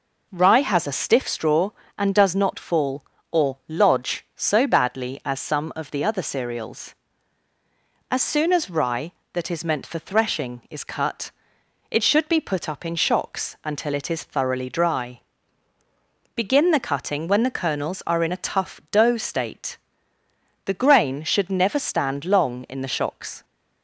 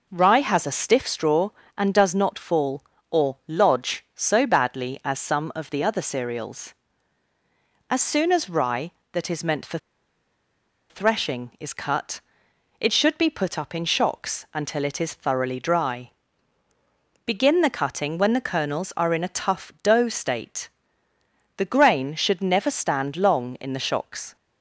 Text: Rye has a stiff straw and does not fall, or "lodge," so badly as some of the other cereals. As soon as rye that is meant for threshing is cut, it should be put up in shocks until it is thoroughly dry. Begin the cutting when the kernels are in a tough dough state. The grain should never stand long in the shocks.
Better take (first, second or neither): first